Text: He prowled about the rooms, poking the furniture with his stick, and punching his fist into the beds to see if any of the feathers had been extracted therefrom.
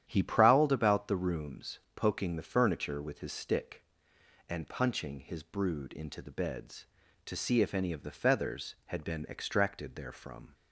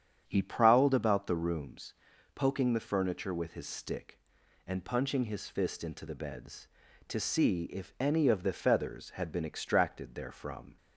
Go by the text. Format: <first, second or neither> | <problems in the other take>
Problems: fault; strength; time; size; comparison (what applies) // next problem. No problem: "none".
second | starts louder than the rest; strong; until 1.0 s; 10.5 dB; strong in the second // says "brood" for "fist"; at 5.4 s